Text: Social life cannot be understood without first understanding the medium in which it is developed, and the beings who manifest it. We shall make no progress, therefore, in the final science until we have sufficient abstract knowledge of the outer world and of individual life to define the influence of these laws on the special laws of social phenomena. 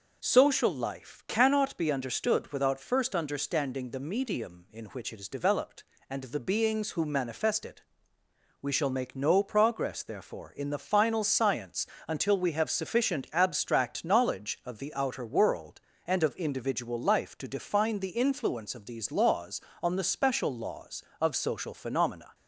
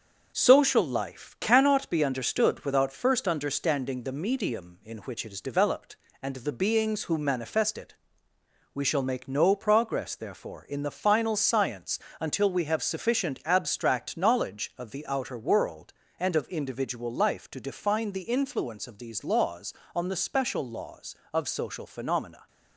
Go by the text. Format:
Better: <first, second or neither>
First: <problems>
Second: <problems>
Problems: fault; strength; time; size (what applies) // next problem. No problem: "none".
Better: first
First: pauses between "science" and "until"; slight; at 11.8 s; 0.20 s long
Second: gets quieter; noticeable; throughout; 4.5 dB // pauses between "science" and "until"; slight; at 11.9 s; 0.20 s long